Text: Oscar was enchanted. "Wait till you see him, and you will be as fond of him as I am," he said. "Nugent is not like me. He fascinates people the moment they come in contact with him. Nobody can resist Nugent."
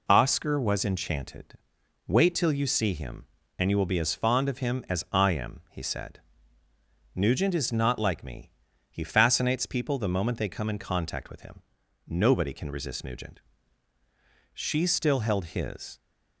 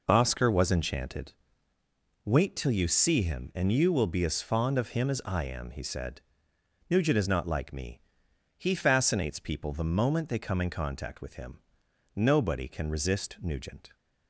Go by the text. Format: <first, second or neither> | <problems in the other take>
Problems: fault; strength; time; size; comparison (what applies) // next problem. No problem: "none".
second | goes on to say "She still held his"; from 14.5 s on; 1.4 s long